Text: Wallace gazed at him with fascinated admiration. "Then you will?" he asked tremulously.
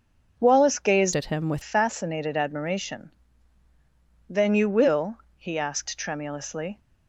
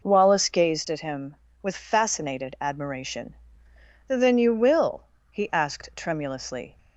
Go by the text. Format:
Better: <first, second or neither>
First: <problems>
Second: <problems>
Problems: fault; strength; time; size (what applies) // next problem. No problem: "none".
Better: second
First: starts louder than the rest; noticeable; until 1.4 s; 6 dB // changes voice from "at" to "with"; from 1.1 to 1.6 s; 0.5 s long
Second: none